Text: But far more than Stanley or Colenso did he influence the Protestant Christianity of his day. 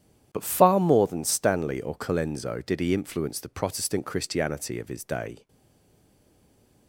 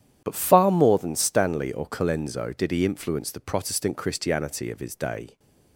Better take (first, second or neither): second